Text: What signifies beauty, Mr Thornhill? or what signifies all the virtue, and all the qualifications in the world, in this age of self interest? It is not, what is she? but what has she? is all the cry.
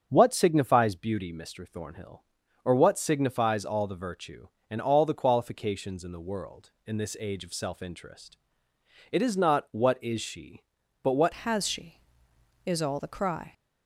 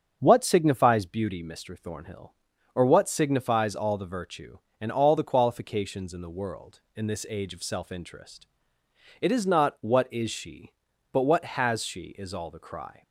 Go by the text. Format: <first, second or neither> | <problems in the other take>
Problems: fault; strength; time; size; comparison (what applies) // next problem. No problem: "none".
second | starts louder than the rest; strong; until 1.1 s; 7 dB; strong in the second // changes voice at "has"; from 11.4 s on; 2.1 s long